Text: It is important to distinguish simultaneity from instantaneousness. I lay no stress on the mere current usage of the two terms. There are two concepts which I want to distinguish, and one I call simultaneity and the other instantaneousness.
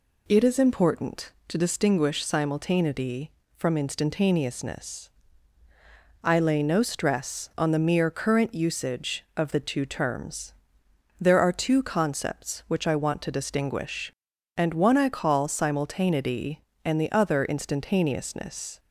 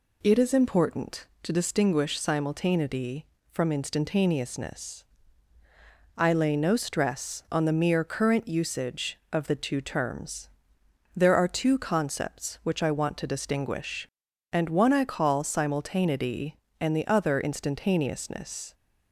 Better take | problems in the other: neither | none

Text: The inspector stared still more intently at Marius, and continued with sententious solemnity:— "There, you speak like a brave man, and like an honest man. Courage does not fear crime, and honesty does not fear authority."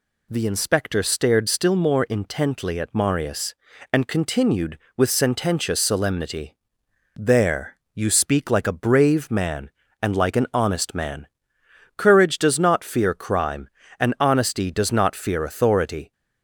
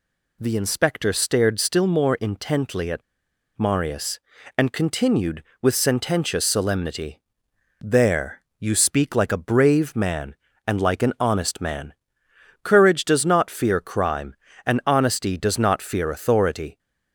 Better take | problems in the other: first | pauses between "at" and "Marius"; noticeable; at 3.0 s; 0.56 s long

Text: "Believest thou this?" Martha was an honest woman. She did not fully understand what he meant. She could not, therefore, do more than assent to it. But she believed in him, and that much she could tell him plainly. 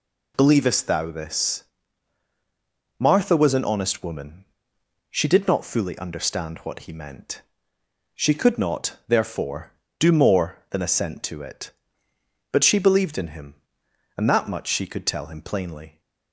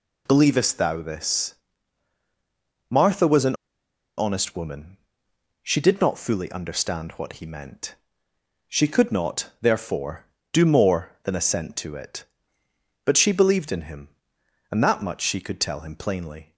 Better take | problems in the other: first | pauses between "an" and "honest"; noticeable; at 3.5 s; 0.63 s long

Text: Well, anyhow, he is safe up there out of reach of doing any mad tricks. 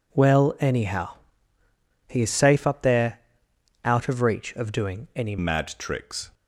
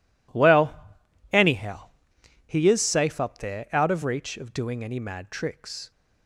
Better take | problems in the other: second | pauses between "there" and "out"; noticeable; at 3.2 s; 0.64 s long // changes voice at "mad"; from 5.3 s on; 1.0 s long

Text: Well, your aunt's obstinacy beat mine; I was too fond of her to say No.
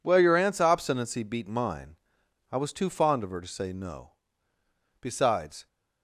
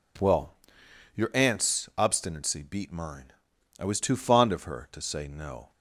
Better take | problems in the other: second | goes on to say "Besides"; noticeable; from 5.0 s on; 0.64 s long

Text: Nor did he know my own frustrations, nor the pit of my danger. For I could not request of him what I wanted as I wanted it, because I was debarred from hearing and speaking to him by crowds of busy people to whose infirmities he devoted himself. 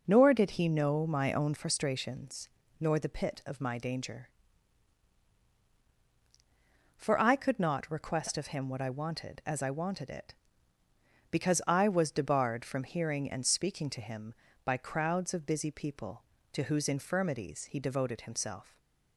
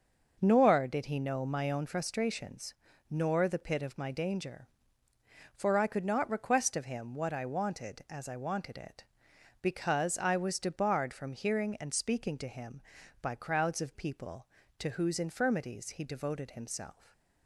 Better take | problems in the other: first | starts louder than the rest; noticeable; until 1.4 s; 6 dB // skips "busy"; at 13.9 s // stays silent after the last word; slight; from 16.9 s on; 0.5 s long

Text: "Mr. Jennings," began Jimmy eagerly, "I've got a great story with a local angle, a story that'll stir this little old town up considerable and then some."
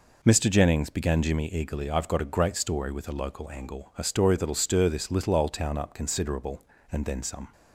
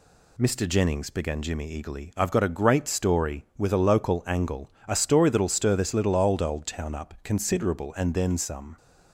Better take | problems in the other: first | says "old" twice; at 6.4 s

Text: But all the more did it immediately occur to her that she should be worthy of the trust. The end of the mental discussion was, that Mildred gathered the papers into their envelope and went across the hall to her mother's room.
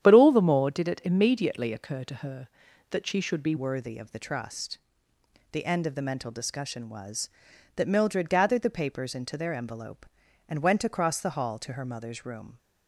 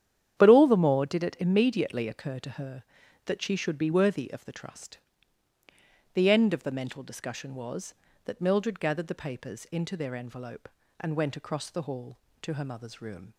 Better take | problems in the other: second | starts louder than the rest; strong; until 1.0 s; 9.5 dB; strong in the second // changes voice at "worthy"; from 3.5 s on; 9.0 s long

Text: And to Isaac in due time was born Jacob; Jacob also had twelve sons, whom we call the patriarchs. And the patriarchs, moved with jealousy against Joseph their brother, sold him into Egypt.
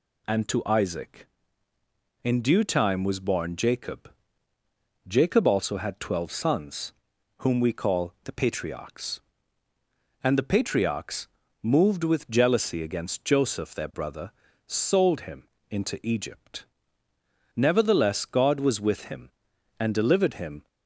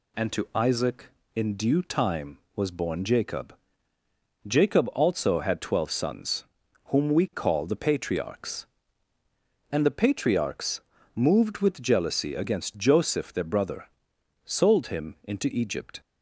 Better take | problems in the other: second | pauses between "him" and "into"; slight; at 15.4 s; 0.24 s long // goes on to say "Nevertheless God was with him and delivered him"; strong; from 17.5 s on; 3.1 s long

